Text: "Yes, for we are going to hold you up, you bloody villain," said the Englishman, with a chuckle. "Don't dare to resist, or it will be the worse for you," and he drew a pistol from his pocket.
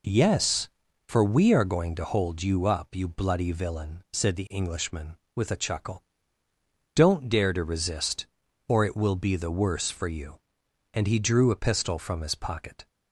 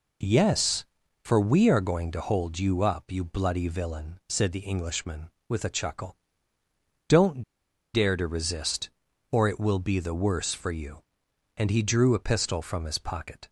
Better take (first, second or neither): first